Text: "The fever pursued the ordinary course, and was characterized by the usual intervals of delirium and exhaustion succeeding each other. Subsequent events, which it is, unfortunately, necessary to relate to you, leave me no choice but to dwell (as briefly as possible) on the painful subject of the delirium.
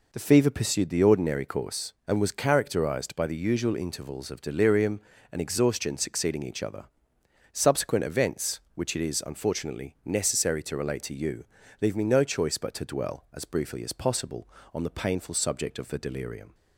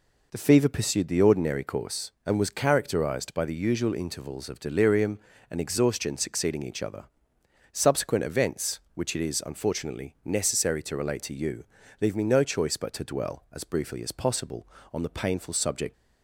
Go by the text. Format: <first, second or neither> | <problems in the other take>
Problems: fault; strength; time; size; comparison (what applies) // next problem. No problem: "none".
first | stops before "of the delirium"; at 15.9 s